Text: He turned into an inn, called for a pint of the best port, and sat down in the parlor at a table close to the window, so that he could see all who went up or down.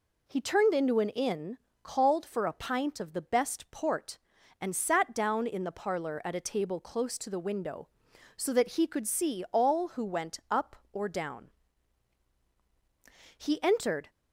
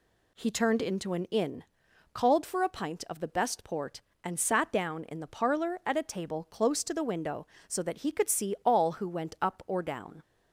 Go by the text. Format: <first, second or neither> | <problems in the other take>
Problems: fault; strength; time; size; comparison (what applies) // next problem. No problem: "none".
second | goes on to say "He entered"; noticeable; from 13.3 s on; 0.72 s long